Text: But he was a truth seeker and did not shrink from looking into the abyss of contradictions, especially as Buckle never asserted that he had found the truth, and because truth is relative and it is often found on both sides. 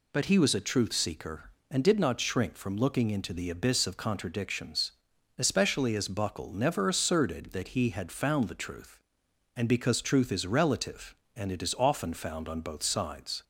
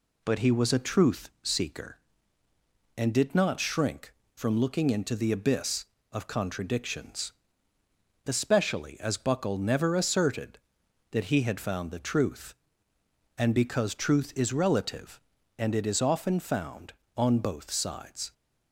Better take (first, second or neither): neither